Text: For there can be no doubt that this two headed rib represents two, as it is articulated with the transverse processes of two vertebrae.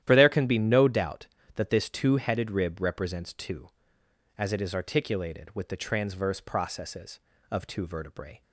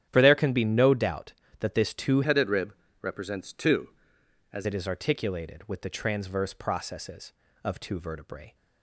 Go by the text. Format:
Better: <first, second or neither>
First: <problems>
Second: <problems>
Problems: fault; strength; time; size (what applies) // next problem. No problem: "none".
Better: first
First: starts louder than the rest; strong; until 1.0 s; 11.5 dB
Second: starts louder than the rest; strong; until 1.1 s; 10.5 dB // changes voice from "headed" to "as"; from 2.2 to 4.6 s; 2.4 s long // pauses between "rib" and "represents"; slight; at 2.7 s; 0.28 s long